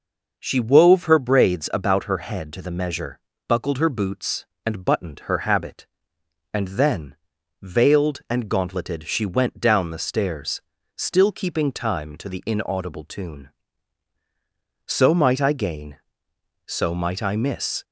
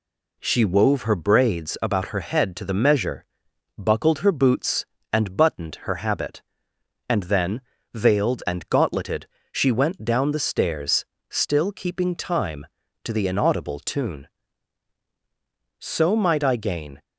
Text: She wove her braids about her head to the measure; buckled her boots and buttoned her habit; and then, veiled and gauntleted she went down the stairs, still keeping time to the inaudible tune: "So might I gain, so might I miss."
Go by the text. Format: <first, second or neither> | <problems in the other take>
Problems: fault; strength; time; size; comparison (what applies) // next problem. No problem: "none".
first | pauses between "gauntleted" and "she"; slight; at 9.2 s; 0.24 s long // stops before "so might I miss"; at 17.0 s